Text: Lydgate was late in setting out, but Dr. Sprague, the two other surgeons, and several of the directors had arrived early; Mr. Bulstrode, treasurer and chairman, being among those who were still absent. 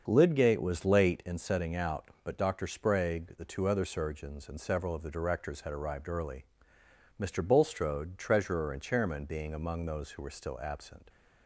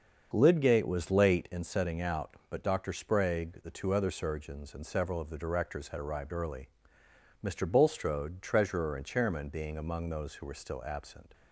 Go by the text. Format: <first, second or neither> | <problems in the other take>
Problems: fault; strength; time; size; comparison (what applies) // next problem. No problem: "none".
neither | starts louder than the rest; the same in both